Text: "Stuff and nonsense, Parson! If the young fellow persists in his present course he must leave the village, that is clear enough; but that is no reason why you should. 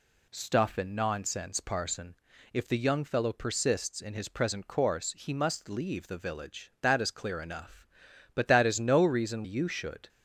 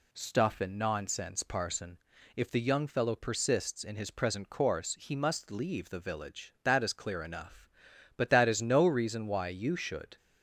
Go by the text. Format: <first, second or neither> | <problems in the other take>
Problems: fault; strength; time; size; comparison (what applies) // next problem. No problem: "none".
second | skips "why"; at 9.4 s